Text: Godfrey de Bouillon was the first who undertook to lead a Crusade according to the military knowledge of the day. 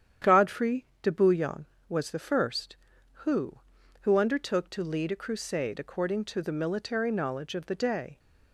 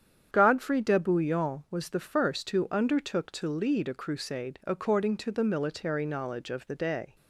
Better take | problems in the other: second | starts louder than the rest; strong; until 1.3 s; 9.5 dB; strong in the second // pauses between "Godfrey" and "de"; slight; at 0.8 s; 0.16 s long // says "who" twice; at 4.0 s

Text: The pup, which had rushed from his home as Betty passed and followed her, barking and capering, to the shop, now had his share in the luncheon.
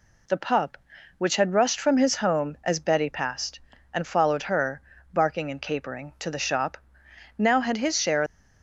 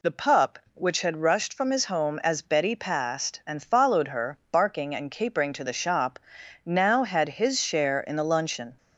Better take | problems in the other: second | stops before "in the luncheon"; at 8.2 s

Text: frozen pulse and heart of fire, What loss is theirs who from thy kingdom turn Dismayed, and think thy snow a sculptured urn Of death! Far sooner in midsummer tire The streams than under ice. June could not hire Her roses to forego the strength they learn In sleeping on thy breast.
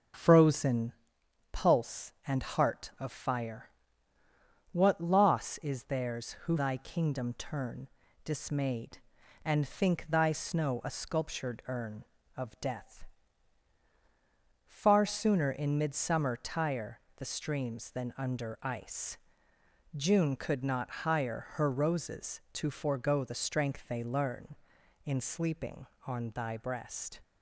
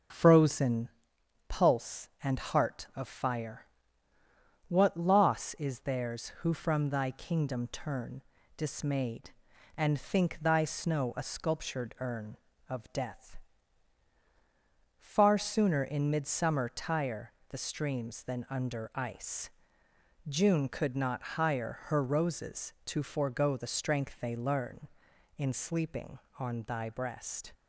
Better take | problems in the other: second | starts louder than the rest; until 1.7 s; 6.5 dB; also in the second // pauses between "frozen" and "pulse"; noticeable; at 0.9 s; 0.58 s long; noticeable in the second // skips "from"; at 6.5 s // pauses between "turn" and "Dismayed"; at 7.8 s; 0.38 s long; also in the second // pauses between "tire" and "The"; slight; at 16.9 s; 0.18 s long; slight in the second

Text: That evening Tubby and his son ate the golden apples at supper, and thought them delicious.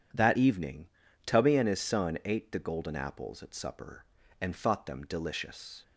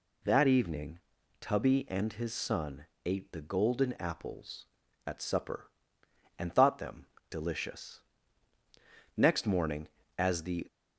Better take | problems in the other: first | pauses between "evening" and "Tubby"; at 1.0 s; 0.40 s long; also in the first // pauses between "son" and "ate"; slight; at 2.8 s; 0.20 s long // pauses between "them" and "delicious"; slight; at 7.0 s; 0.22 s long // goes on to say "Next morning as the"; from 9.1 s on; 1.4 s long

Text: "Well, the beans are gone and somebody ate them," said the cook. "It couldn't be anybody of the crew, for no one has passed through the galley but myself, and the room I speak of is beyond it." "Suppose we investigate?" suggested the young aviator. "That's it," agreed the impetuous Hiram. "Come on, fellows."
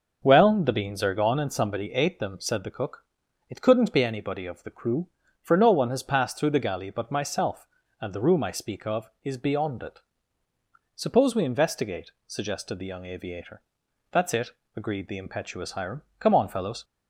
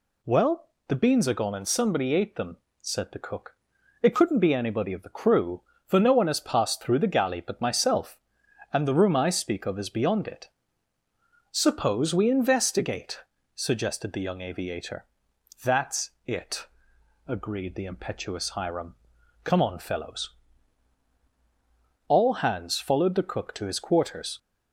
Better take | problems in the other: first | goes on to say "All hands followed the cook to his quarters"; strong; from 22.0 s on; 2.3 s long

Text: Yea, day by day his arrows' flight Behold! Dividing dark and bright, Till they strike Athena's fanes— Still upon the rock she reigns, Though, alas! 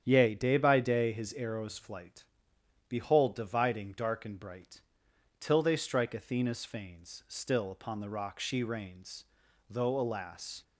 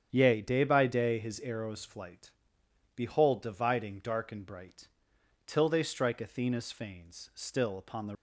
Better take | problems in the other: first | starts louder than the rest; strong; until 1.1 s; 8.5 dB; strong in the first // pauses between "flight" and "Behold"; noticeable; at 2.3 s; 0.64 s long; noticeable in the first // stops before "rock she reigns Though alas"; at 8.1 s

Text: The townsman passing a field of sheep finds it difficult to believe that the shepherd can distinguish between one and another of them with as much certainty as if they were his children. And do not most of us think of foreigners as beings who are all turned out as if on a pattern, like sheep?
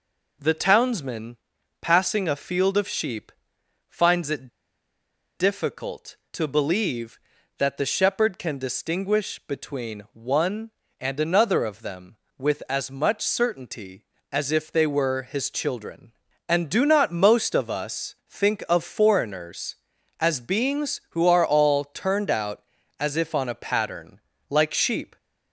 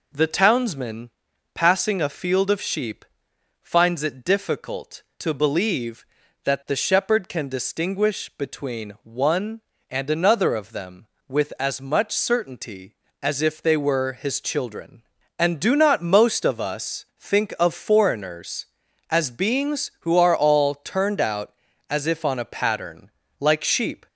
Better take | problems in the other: second | pauses between "townsman" and "passing"; noticeable; at 1.3 s; 0.46 s long; noticeable in the second // pauses between "sheep" and "finds"; noticeable; at 3.2 s; 0.60 s long; noticeable in the second // pauses between "it" and "difficult"; noticeable; at 4.4 s; 0.87 s long

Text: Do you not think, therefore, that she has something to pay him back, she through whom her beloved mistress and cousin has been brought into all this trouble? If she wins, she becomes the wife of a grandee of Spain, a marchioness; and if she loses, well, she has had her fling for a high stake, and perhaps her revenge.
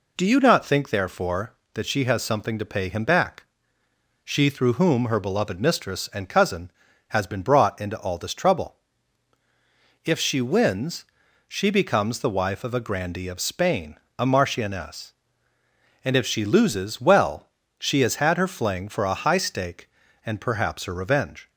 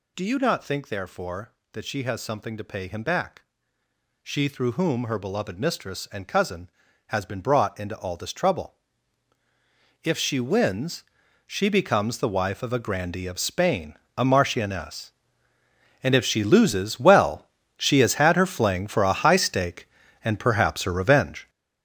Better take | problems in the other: first | gets louder; strong; throughout; 9 dB

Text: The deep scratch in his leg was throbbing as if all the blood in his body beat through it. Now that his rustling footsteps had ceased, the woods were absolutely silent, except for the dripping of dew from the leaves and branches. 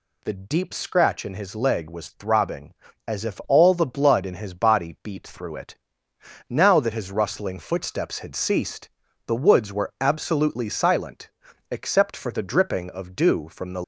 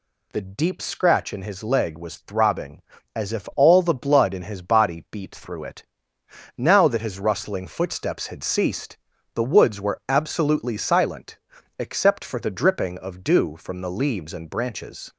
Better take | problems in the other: second | stops before "leaves and branches"; at 13.8 s

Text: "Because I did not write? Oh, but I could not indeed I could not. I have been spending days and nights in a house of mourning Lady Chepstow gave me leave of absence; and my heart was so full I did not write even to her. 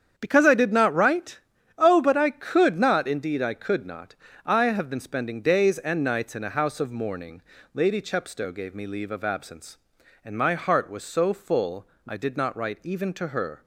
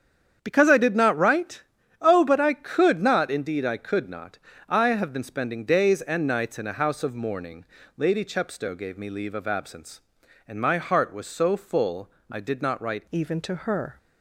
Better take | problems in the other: first | starts louder than the rest; strong; until 1.4 s; 8.5 dB; strong in the first // pauses between "mourning" and "Lady"; slight; at 7.6 s; 0.32 s long; slight in the first // pauses between "full" and "I"; slight; at 12.0 s; 0.22 s long; slight in the first // changes voice at "even"; from 13.1 s on; 0.8 s long

